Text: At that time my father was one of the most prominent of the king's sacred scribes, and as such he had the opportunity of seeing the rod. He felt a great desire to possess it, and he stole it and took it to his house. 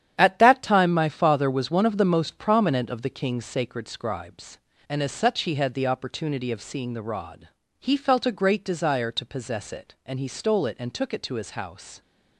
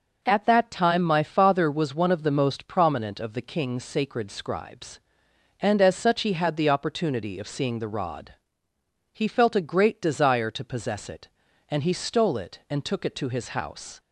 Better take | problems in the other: second | gets quieter; strong; throughout; 9 dB

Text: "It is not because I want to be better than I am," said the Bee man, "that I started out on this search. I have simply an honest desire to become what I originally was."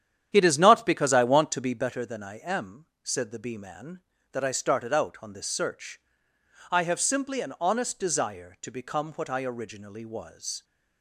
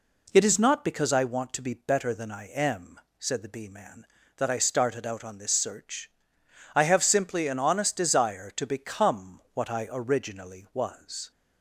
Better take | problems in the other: second | starts louder than the rest; strong; until 1.9 s; 9.5 dB

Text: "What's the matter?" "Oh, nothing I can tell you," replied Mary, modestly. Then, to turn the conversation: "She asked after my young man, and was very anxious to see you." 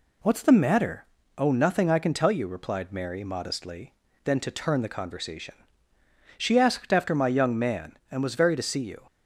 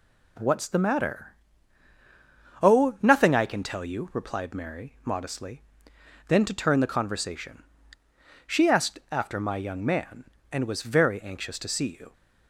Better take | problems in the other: second | skips "anxious"; at 8.5 s

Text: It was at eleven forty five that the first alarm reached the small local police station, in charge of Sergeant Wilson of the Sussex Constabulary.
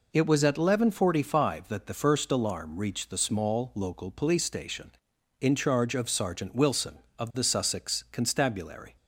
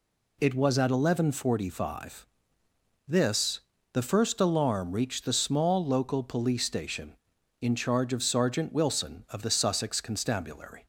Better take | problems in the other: first | says "this" for "that"; at 3.0 s

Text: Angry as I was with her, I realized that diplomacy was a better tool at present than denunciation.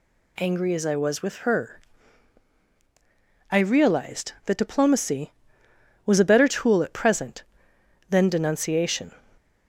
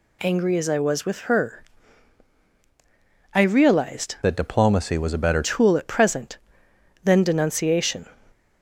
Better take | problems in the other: first | changes voice from "that" to "better"; from 4.2 to 5.4 s; 1.2 s long

